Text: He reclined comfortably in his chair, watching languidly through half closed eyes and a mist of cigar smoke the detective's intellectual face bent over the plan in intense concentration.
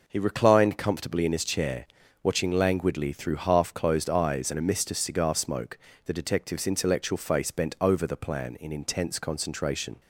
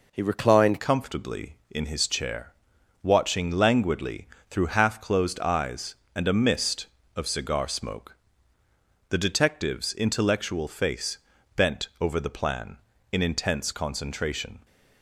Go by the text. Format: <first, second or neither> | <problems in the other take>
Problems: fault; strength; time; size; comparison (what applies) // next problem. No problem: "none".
first | changes voice at "comfortably"; from 0.7 s on; 13.9 s long // pauses between "languidly" and "through"; slight; at 4.2 s; 0.22 s long // pauses between "smoke" and "the"; noticeable; at 8.1 s; 0.98 s long; slight in the first // pauses between "face" and "bent"; slight; at 11.1 s; 0.36 s long